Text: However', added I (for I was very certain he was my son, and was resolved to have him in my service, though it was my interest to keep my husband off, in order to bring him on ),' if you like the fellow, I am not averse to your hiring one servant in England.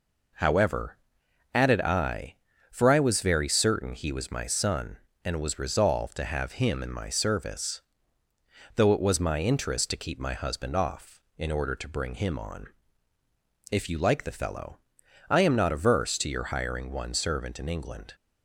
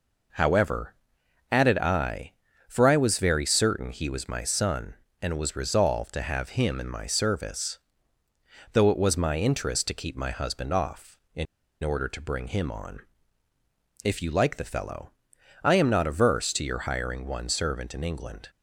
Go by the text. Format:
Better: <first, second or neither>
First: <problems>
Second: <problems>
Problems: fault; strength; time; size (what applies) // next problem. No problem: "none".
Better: first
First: none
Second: pauses between "in" and "order"; at 11.4 s; 0.38 s long